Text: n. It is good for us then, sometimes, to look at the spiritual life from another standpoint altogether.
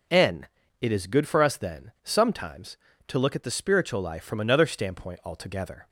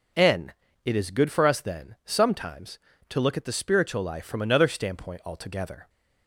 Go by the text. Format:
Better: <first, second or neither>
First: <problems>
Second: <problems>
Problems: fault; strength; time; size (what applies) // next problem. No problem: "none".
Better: neither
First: none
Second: none